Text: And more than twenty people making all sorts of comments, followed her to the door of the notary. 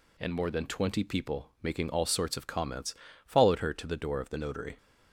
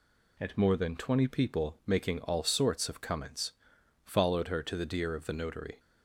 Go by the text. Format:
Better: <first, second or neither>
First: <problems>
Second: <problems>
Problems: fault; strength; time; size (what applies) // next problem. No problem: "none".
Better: first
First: none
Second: says "deer" for "door"; at 4.8 s